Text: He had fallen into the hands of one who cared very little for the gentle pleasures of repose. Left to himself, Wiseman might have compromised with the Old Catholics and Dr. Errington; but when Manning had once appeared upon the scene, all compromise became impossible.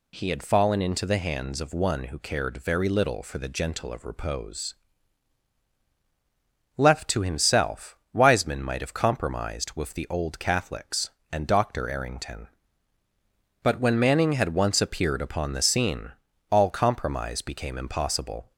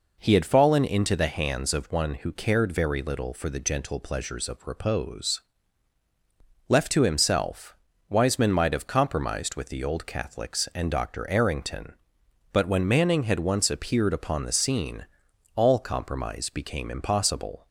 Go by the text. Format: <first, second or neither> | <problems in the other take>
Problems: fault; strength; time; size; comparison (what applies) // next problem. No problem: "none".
second | skips "pleasures"; at 3.9 s